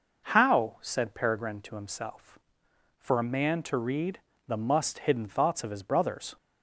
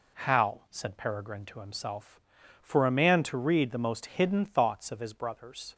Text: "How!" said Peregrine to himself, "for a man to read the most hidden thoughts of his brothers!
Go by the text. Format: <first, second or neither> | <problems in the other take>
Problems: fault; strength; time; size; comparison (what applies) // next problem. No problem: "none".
second | pauses between "read" and "the"; slight; at 4.2 s; 0.26 s long // says "must" for "most"; at 4.5 s